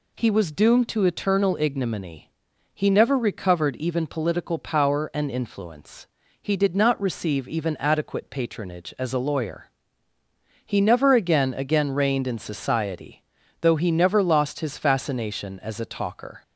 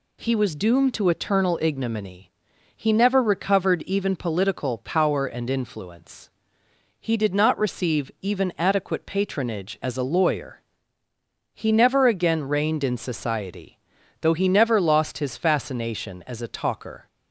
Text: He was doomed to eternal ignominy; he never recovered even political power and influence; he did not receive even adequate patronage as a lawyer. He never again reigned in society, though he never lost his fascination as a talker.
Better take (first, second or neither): second